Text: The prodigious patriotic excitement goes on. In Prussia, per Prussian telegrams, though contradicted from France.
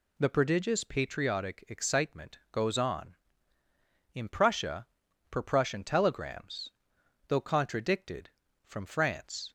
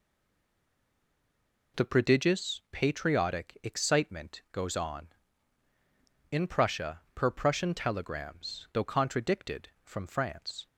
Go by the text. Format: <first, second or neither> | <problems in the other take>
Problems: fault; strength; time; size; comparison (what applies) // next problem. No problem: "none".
first | stays silent before the first word; noticeable; until 1.7 s; 1.7 s long